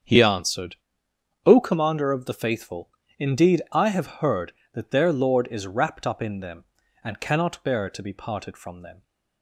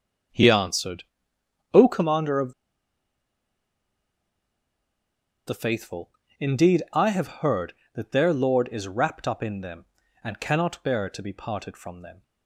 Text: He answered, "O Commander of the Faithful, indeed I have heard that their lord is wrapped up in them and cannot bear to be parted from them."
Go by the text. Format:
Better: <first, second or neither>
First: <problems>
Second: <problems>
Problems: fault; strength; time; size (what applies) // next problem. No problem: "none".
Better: first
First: starts louder than the rest; strong; until 1.7 s; 7.5 dB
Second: starts louder than the rest; strong; until 2.0 s; 7.5 dB // pauses between "of" and "the"; strong; at 2.5 s; 2.9 s long